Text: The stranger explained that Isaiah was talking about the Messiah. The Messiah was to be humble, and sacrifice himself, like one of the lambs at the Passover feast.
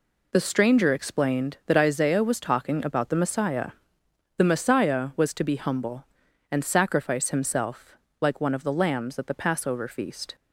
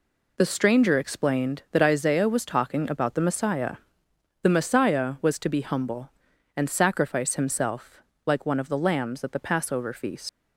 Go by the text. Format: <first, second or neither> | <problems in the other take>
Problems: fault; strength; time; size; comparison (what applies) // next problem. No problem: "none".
first | leaves "feast" unfinished; at 10.2 s; 110 ms